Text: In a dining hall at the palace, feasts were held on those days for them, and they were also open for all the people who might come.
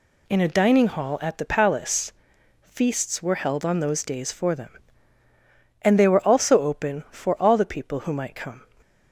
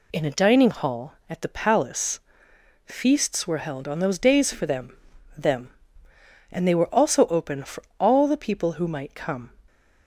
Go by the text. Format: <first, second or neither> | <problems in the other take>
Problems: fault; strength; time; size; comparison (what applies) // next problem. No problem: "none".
first | says "them" twice; at 5.3 s // pauses between "for" and "all"; slight; at 7.8 s; 0.16 s long